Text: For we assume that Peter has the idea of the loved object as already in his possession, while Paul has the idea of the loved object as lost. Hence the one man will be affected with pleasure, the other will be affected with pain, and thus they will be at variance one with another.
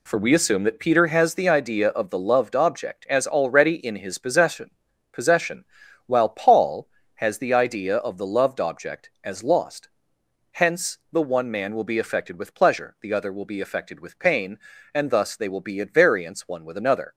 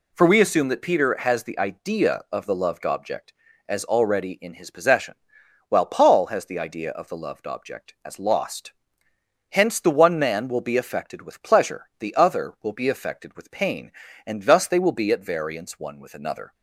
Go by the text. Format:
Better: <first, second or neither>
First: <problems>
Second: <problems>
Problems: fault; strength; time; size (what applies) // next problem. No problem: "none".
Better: second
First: says "possession" twice; at 5.1 s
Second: none